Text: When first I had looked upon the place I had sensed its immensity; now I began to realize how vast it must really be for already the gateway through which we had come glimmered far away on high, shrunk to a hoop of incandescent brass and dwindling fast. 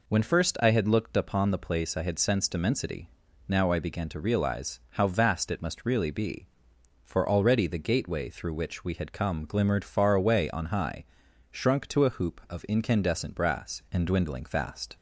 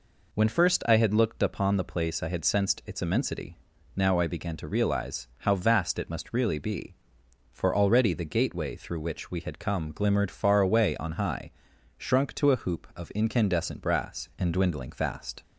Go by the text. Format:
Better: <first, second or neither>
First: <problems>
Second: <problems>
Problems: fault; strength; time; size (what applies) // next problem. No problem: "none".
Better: second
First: skips "its"; at 2.5 s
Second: none